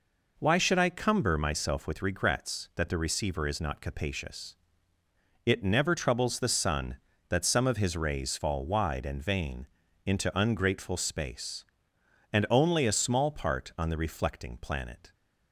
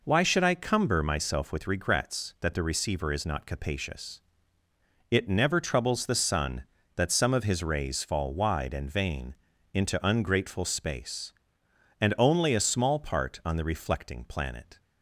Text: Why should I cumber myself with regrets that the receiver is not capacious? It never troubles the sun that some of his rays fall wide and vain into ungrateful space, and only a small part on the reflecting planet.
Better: neither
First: pauses between "vain" and "into"; at 9.6 s; 0.40 s long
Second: pauses between "vain" and "into"; at 9.3 s; 0.40 s long

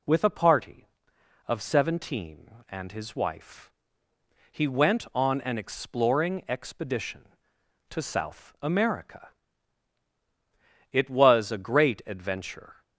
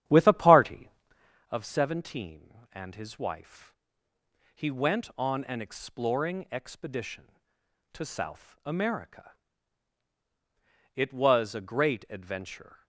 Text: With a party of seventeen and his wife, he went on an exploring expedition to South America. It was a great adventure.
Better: first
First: none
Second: starts louder than the rest; strong; until 1.5 s; 10.5 dB

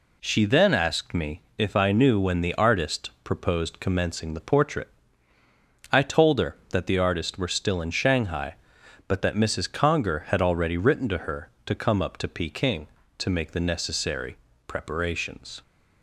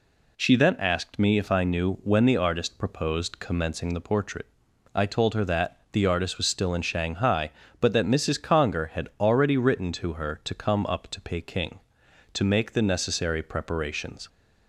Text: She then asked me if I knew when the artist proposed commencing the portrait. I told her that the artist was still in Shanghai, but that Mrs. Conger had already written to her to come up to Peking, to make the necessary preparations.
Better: second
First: pauses between "me" and "if"; slight; at 1.3 s; 0.16 s long // says "were" for "was"; at 7.3 s // pauses between "necessary" and "preparations"; slight; at 14.3 s; 0.32 s long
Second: none

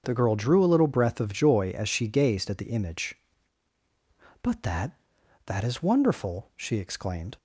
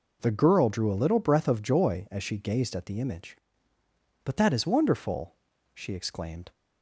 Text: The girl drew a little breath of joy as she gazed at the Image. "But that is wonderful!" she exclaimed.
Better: second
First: starts louder than the rest; until 1.0 s; 7 dB // says "that" twice; at 5.4 s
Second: none

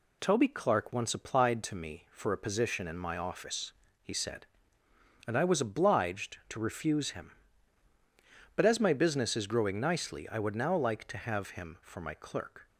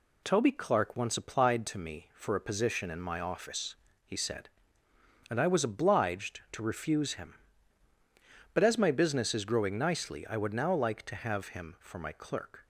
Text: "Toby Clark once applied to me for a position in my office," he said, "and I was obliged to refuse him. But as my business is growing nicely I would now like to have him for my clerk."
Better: neither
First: none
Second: none

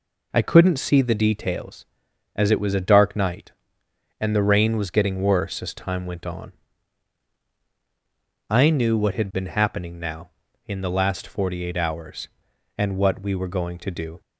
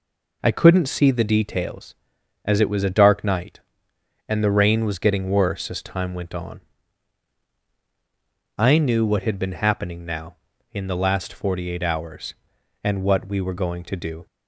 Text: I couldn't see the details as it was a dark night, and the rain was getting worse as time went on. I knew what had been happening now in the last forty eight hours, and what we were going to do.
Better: neither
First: none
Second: none

